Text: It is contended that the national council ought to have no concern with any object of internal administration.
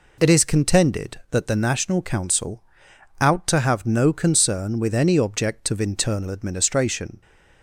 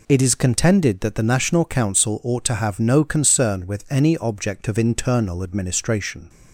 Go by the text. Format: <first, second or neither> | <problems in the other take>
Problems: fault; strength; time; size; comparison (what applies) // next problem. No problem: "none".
second | says "out" for "ought"; at 3.2 s